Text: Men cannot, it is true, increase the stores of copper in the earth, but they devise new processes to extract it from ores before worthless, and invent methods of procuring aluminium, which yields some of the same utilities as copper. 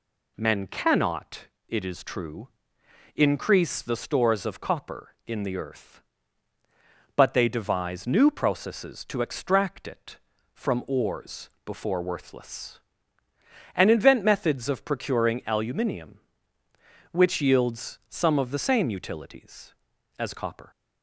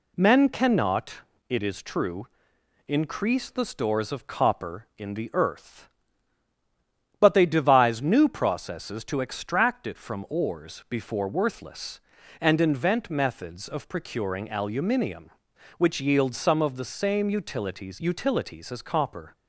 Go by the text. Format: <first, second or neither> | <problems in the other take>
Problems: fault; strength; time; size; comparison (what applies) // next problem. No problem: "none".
first | says "utilities" twice; at 18.0 s